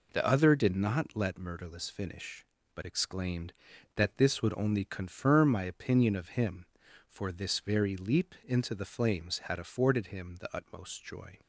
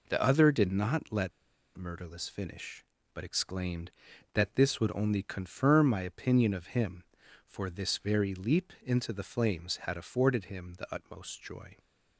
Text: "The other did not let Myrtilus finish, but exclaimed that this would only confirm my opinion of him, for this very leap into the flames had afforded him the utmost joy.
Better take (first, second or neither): first